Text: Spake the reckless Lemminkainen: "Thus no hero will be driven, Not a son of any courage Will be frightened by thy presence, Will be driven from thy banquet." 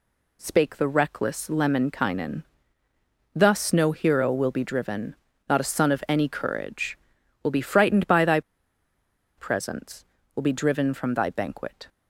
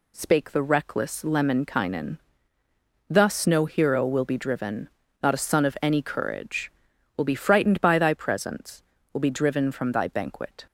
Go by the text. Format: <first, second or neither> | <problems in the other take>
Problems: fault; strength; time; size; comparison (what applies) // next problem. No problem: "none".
second | pauses between "thy" and "presence"; noticeable; at 8.4 s; 0.97 s long